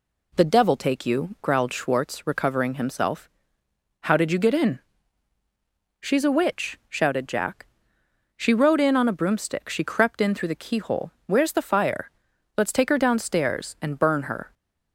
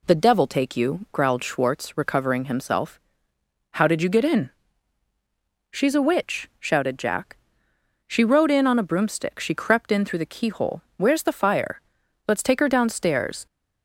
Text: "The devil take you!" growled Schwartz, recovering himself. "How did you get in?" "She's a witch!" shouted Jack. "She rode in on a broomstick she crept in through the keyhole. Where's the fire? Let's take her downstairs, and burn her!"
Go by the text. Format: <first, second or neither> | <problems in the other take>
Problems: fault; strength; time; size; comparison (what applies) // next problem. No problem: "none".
first | stops before "and burn her"; at 13.4 s